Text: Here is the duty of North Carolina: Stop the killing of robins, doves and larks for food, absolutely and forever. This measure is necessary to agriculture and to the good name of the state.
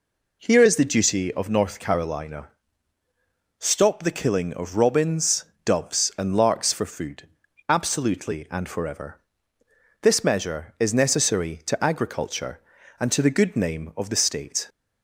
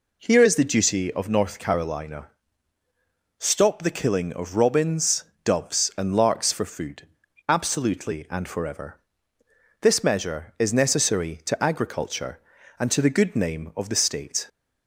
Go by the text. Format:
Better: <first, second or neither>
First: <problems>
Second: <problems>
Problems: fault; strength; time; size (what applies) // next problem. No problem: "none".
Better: neither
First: none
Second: none